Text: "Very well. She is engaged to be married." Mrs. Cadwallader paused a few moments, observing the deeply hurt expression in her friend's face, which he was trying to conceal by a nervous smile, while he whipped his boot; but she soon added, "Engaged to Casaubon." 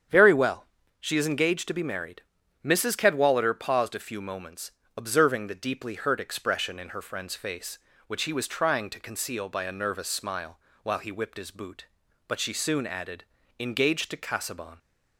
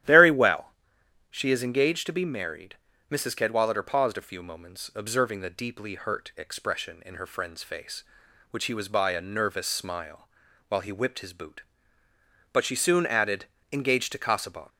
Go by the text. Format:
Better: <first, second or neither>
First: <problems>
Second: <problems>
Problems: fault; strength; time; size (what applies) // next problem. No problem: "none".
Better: first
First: starts louder than the rest; strong; until 1.4 s; 8.5 dB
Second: starts louder than the rest; strong; until 1.6 s; 12 dB // skips "trying to conceal"; at 8.8 s